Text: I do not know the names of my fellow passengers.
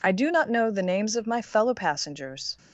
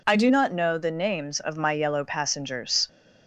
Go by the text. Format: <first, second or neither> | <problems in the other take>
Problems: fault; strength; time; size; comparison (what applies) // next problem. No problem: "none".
first | says "yellow" for "fellow"; at 1.7 s